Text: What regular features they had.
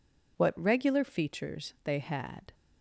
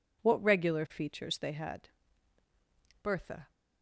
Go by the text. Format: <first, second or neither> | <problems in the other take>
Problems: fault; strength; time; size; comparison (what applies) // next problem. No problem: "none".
first | goes on to say "Bertha"; slight; from 3.0 s on; 0.48 s long